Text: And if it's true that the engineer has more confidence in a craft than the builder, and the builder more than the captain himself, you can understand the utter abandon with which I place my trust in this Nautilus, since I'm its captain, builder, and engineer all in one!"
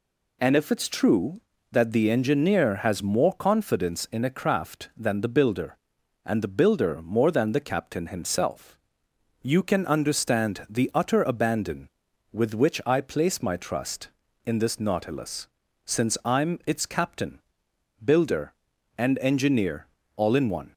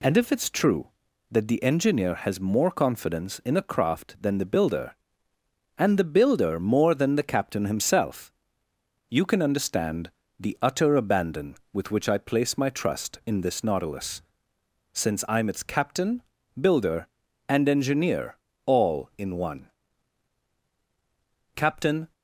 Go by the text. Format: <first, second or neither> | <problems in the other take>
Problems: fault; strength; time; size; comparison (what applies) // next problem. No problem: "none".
first | pauses between "understand" and "the"; slight; at 10.1 s; 0.30 s long // pauses between "engineer" and "all"; slight; at 18.3 s; 0.30 s long; slight in the first // goes on to say "Captain"; from 21.5 s on; 0.58 s long